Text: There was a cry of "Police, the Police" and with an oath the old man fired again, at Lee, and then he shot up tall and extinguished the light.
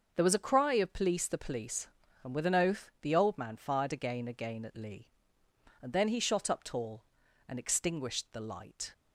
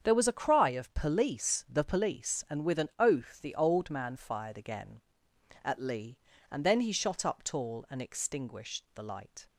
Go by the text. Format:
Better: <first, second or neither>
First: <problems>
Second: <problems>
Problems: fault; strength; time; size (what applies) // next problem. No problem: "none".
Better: second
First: starts louder than the rest; until 1.1 s; 6.5 dB // says "again" twice; at 4.2 s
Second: starts louder than the rest; strong; until 1.1 s; 7.5 dB